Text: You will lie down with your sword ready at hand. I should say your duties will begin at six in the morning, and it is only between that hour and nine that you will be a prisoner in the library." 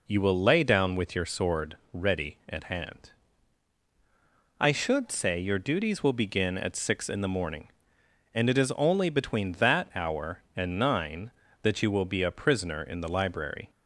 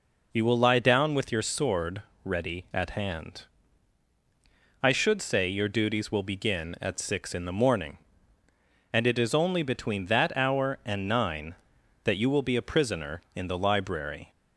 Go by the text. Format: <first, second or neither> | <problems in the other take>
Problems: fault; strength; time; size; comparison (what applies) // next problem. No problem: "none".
second | says "lay" for "lie"; at 0.3 s // pauses between "sword" and "ready"; slight; at 1.7 s; 0.16 s long; slight in the second